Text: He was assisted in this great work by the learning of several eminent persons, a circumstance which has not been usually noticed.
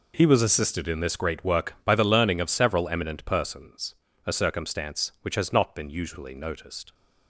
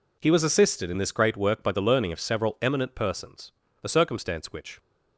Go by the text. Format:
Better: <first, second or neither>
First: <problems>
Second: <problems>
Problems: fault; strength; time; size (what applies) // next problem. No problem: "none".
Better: first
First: none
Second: stops before "has not been usually noticed"; at 4.7 s